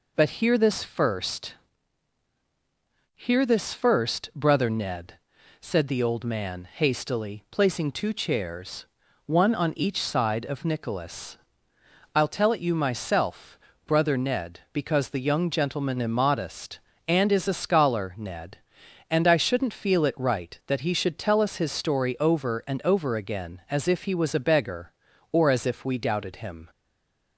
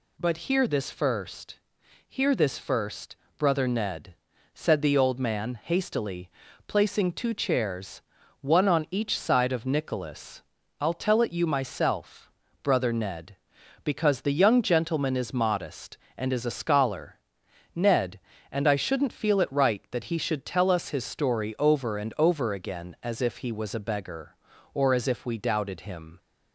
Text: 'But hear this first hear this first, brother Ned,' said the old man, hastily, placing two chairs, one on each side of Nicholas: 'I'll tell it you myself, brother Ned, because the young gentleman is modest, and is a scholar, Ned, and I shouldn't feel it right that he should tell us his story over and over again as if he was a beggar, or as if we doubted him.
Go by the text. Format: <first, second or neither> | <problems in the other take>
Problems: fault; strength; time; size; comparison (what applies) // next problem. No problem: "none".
second | pauses between "first" and "hear"; strong; at 1.5 s; 1.6 s long; noticeable in the second // stays silent after the last word; slight; from 26.6 s on; 0.7 s long